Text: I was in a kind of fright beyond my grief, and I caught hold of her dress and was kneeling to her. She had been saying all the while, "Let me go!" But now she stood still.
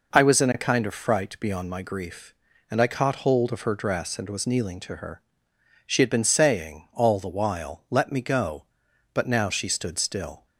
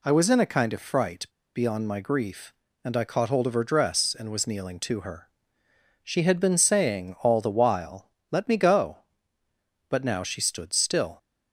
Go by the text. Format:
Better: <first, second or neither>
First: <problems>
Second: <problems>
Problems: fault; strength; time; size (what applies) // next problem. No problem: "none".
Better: first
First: none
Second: pauses between "fright" and "beyond"; slight; at 1.2 s; 0.29 s long